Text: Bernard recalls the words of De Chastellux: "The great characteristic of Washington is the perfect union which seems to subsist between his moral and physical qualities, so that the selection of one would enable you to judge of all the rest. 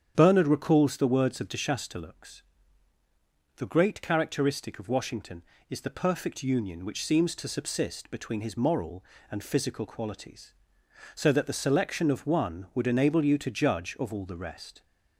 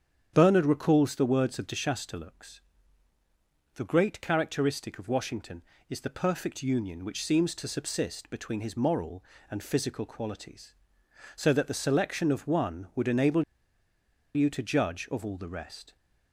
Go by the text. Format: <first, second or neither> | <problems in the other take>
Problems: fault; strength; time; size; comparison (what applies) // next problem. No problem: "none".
first | starts louder than the rest; strong; until 1.3 s; 8.5 dB; strong in the first // pauses between "enable" and "you"; noticeable; at 13.4 s; 0.93 s long